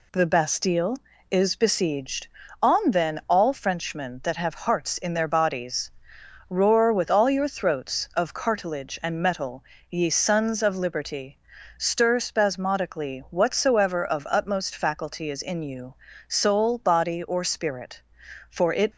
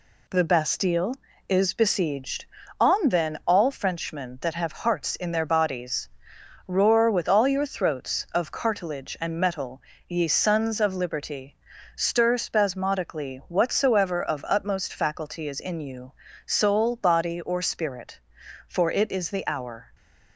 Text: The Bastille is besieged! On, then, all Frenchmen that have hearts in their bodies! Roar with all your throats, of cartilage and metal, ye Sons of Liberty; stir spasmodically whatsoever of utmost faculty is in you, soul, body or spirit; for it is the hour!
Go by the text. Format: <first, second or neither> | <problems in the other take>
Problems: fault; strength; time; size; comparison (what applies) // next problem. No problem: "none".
second | stops before "is the hour"; at 18.9 s